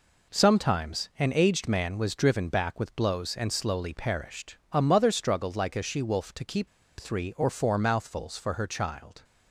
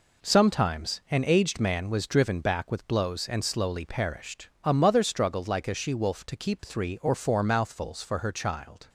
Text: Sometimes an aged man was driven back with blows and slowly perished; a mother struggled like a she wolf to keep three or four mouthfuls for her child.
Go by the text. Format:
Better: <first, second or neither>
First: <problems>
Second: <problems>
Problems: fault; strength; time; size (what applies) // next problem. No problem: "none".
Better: second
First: pauses between "keep" and "three"; slight; at 6.6 s; 0.29 s long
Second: none